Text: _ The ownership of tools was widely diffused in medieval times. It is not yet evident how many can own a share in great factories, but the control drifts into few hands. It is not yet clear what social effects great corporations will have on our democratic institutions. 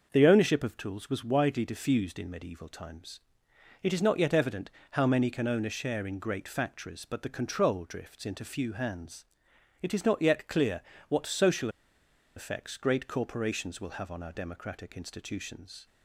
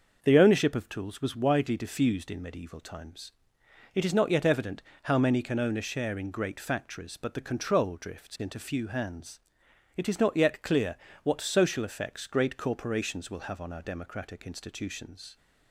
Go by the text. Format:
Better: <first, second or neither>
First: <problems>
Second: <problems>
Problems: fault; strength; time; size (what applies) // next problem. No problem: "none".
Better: second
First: starts louder than the rest; noticeable; until 1.1 s; 6 dB // pauses between "evident" and "how"; slight; at 4.7 s; 0.22 s long // pauses between "clear" and "what"; slight; at 10.8 s; 0.28 s long // pauses between "social" and "effects"; noticeable; at 11.6 s; 0.67 s long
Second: starts louder than the rest; noticeable; until 1.2 s; 6 dB // pauses between "evident" and "how"; slight; at 4.8 s; 0.22 s long // pauses between "clear" and "what"; slight; at 10.9 s; 0.28 s long